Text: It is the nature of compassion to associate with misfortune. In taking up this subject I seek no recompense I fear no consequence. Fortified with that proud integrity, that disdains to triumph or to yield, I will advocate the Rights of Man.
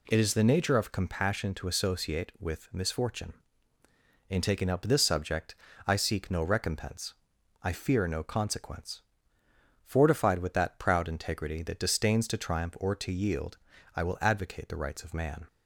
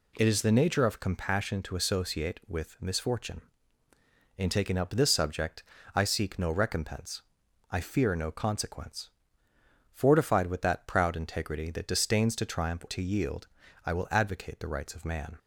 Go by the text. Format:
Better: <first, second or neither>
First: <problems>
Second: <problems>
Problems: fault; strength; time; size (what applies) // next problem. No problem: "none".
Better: first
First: pauses between "subject" and "I"; slight; at 5.5 s; 0.30 s long // pauses between "recompense" and "I"; noticeable; at 7.1 s; 0.48 s long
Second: pauses between "subject" and "I"; slight; at 5.6 s; 0.30 s long // pauses between "recompense" and "I"; noticeable; at 7.2 s; 0.48 s long // skips "or"; at 12.8 s